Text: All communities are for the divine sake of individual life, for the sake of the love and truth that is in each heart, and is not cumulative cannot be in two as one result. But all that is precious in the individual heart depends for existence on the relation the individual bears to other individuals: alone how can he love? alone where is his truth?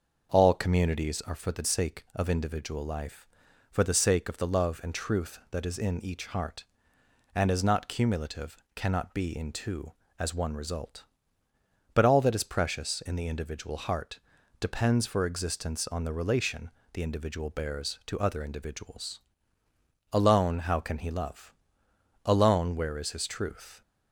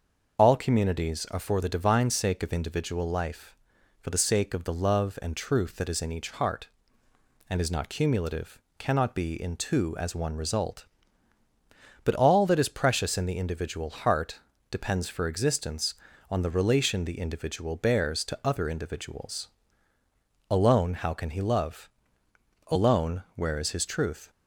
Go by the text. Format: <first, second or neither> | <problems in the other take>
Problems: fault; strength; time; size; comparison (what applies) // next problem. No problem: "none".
second | starts louder than the rest; noticeable; until 1.3 s; 6 dB; also in the second // skips "divine"; at 1.6 s // pauses between "cumulative" and "cannot"; slight; at 8.5 s; 0.18 s long; slight in the second // pauses between "heart" and "depends"; at 14.1 s; 0.42 s long; slight in the second // pauses between "relation" and "the"; slight; at 16.6 s; 0.24 s long